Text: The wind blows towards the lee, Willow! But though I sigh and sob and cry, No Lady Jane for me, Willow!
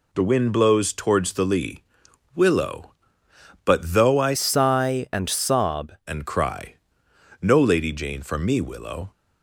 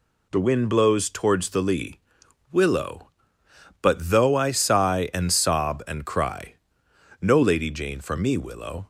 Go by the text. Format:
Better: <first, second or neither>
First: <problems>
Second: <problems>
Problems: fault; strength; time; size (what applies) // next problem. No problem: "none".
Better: second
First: changes voice from "sigh" to "sob"; from 4.3 to 5.9 s; 1.6 s long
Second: none